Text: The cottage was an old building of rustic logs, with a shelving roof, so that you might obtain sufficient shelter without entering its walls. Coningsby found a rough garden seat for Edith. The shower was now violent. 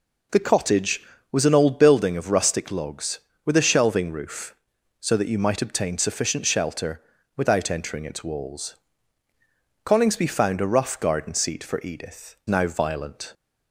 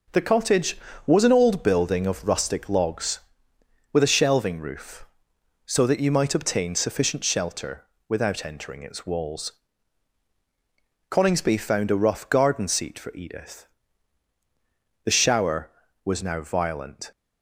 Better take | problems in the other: second | pauses between "shelter" and "without"; slight; at 7.0 s; 0.34 s long; slight in the second // skips "The shower was"; at 12.4 s

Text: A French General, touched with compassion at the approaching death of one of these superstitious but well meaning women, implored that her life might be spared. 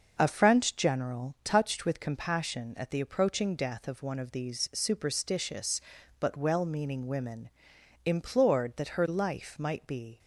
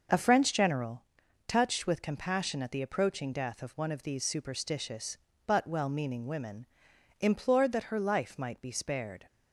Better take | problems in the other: second | stops before "spared"; at 10.1 s

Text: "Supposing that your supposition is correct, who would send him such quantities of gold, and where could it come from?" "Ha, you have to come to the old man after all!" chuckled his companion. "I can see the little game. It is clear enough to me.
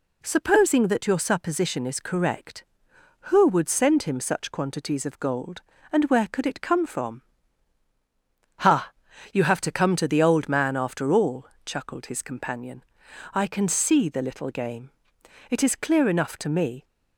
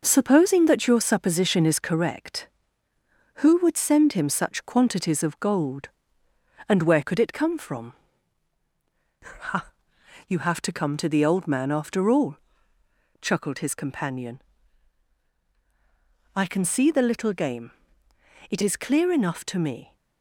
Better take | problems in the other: first | gets quieter; noticeable; throughout; 5.5 dB

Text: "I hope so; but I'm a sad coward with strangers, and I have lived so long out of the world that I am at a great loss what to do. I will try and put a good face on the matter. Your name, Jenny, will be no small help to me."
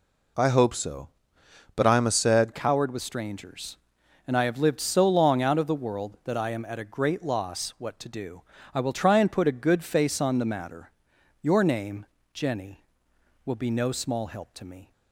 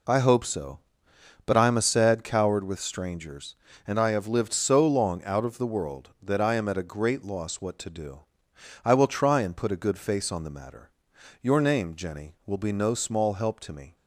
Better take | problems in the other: second | changes voice at "coward"; from 2.5 s on; 12.4 s long

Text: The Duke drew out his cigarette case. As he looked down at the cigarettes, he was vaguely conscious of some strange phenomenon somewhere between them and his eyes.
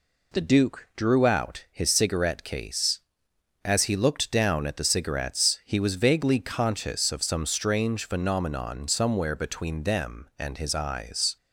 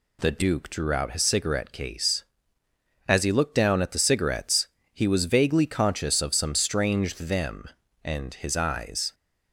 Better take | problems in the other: first | skips "phenomenon somewhere between"; at 7.1 s

